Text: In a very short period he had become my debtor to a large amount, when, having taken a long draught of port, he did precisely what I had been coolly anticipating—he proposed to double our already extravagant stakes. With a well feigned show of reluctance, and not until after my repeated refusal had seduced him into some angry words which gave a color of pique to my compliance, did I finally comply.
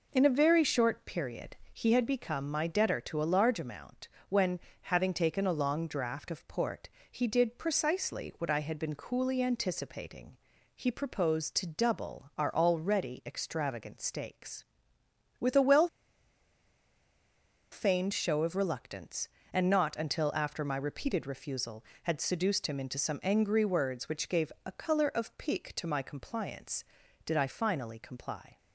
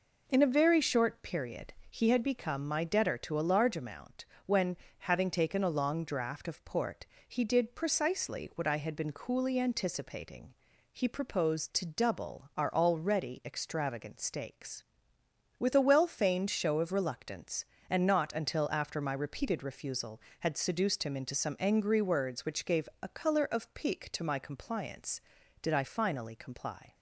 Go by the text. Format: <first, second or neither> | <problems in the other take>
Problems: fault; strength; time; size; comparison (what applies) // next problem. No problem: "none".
second | pauses between "period" and "he"; slight; at 1.5 s; 0.16 s long; slight in the second // pauses between "well" and "feigned"; strong; at 15.8 s; 1.8 s long